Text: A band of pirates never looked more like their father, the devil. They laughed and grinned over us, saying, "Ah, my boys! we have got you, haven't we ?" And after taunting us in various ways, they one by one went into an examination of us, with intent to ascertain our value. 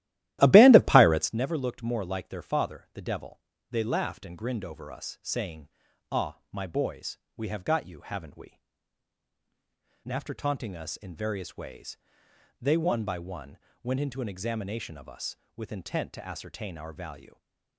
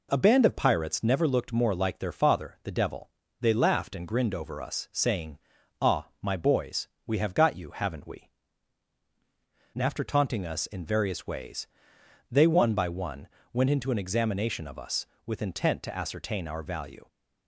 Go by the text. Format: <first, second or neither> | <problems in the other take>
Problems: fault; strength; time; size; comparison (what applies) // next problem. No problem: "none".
second | starts louder than the rest; strong; until 1.3 s; 15 dB // pauses between "one" and "went"; slight; at 13.5 s; 0.26 s long; slight in the second